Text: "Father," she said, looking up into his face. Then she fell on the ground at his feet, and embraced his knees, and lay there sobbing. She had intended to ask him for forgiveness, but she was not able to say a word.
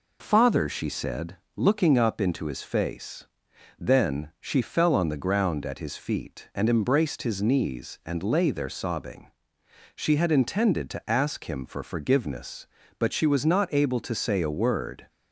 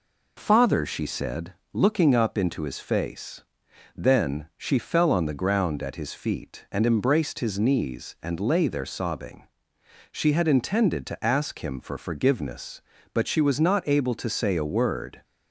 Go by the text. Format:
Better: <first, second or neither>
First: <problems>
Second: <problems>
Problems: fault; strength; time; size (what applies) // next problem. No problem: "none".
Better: neither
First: none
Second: none